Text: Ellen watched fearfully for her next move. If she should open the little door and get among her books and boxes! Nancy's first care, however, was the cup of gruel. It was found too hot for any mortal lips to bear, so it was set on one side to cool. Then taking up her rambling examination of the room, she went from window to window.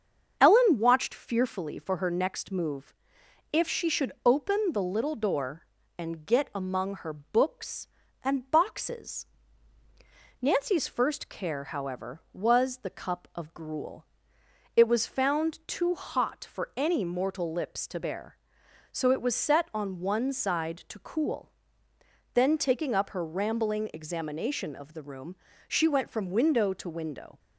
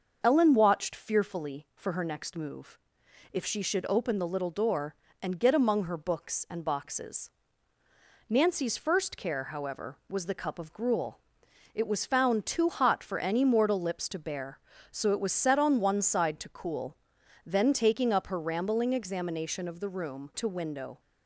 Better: first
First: starts louder than the rest; until 1.4 s; 7 dB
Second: starts louder than the rest; until 1.2 s; 6.5 dB // skips "she went from window"; at 20.3 s

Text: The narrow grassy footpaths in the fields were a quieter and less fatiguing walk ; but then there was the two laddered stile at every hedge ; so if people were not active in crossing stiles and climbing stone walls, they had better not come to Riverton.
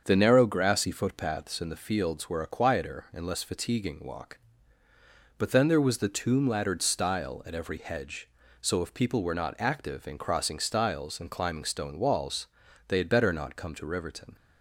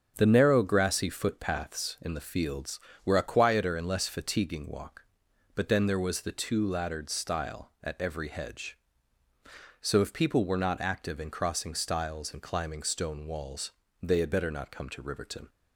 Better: second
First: starts louder than the rest; until 1.0 s; 7 dB // says "tomb" for "two"; at 6.0 s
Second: starts louder than the rest; strong; until 1.1 s; 7.5 dB

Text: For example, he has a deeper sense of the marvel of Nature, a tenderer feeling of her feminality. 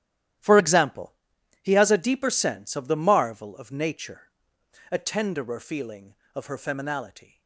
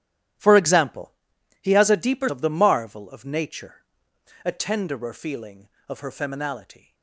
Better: first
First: starts louder than the rest; strong; until 1.9 s; 12.5 dB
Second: starts louder than the rest; strong; until 1.8 s; 12 dB // skips "sense"; at 2.2 s

